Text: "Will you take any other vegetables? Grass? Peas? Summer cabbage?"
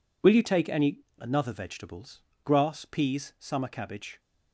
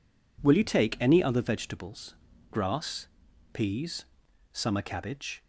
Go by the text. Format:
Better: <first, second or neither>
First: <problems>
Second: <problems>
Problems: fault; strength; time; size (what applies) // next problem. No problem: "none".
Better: second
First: says "another" for "other"; at 1.1 s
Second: none